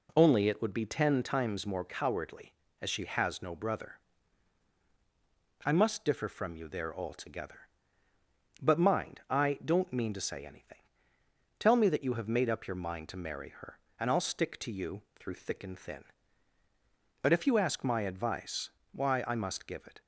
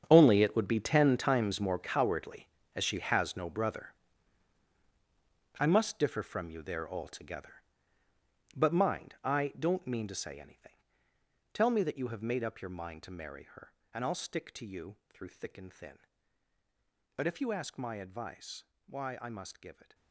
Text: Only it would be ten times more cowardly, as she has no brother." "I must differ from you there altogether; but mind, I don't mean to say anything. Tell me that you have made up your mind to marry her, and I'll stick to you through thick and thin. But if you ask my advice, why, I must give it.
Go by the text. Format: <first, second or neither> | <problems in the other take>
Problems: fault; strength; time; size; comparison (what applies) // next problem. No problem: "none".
first | gets quieter; strong; throughout; 15.5 dB